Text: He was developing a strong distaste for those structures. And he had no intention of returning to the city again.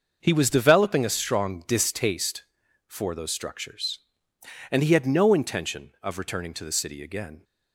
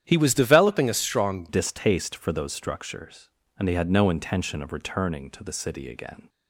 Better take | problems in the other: first | starts louder than the rest; strong; until 1.0 s; 10 dB; also in the first // changes voice at "distaste"; from 1.4 s on; 4.8 s long

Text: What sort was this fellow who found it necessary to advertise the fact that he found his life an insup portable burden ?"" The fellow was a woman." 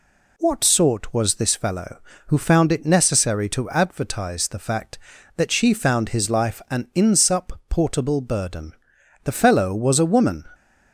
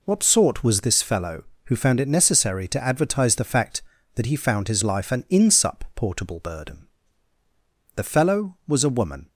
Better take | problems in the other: second | says "she" for "he"; at 5.5 s

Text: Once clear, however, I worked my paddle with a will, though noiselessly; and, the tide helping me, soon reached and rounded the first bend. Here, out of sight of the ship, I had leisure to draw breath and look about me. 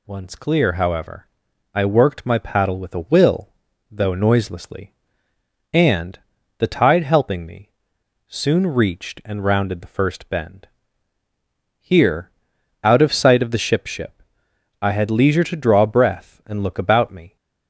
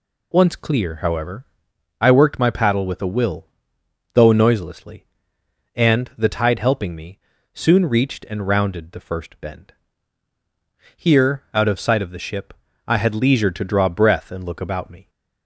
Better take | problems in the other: second | says "ship" twice; at 13.8 s

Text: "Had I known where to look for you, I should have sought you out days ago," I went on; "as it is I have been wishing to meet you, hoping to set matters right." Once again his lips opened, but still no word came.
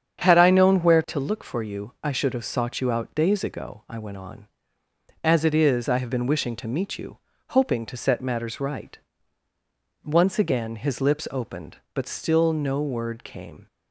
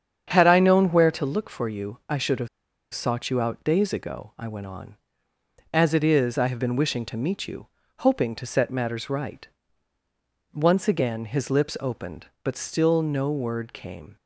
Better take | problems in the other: first | starts louder than the rest; strong; until 1.3 s; 8 dB; strong in the first // pauses between "have" and "sought"; at 2.4 s; 0.45 s long

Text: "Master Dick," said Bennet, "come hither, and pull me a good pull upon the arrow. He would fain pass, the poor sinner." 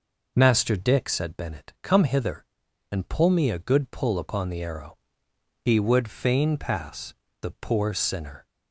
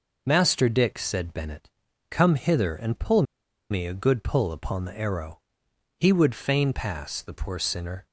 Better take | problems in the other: first | pauses between "pull" and "me"; noticeable; at 3.2 s; 0.47 s long

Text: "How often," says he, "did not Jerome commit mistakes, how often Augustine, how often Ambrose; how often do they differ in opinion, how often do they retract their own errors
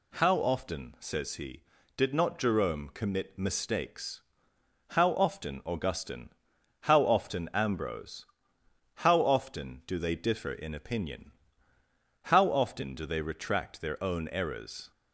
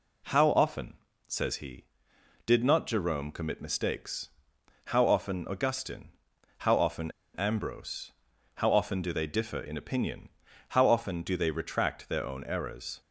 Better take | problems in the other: first | pauses between "often" and "Ambrose"; slight; at 7.1 s; 0.23 s long

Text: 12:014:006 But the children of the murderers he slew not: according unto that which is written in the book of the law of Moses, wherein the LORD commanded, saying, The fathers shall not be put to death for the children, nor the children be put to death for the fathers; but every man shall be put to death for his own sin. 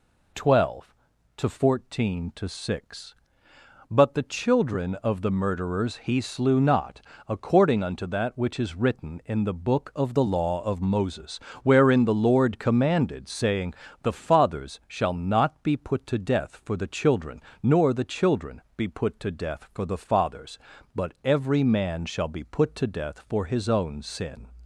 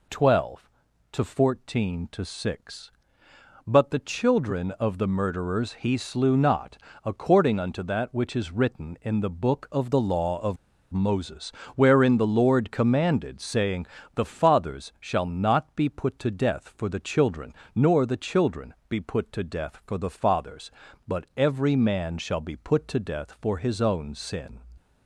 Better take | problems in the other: first | pauses between "of" and "Moses"; slight; at 10.5 s; 0.35 s long // pauses between "children" and "be"; slight; at 18.7 s; 0.16 s long; slight in the first

